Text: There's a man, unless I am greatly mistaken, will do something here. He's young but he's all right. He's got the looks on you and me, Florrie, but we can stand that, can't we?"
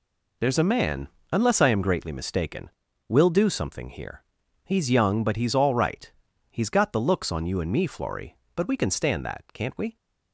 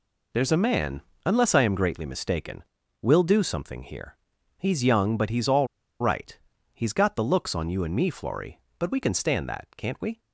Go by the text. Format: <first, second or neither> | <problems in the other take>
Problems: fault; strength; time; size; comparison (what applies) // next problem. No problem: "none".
first | pauses between "all" and "right"; slight; at 5.6 s; 0.33 s long